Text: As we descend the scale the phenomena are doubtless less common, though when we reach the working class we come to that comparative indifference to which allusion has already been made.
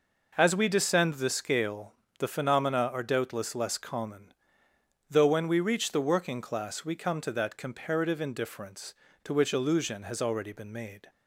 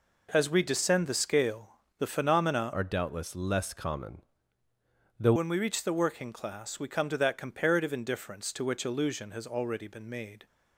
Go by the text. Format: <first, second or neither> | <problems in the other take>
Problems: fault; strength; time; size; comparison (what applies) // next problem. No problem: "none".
first | pauses between "scale" and "the"; slight; at 1.7 s; 0.20 s long; slight in the first // changes voice from "are" to "though"; from 2.7 to 5.3 s; 2.6 s long